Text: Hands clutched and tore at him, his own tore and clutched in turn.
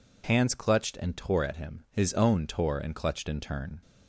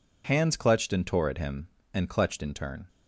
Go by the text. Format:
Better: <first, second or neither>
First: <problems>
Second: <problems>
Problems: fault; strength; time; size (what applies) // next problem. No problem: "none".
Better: first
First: none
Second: skips "his own tore"; at 1.8 s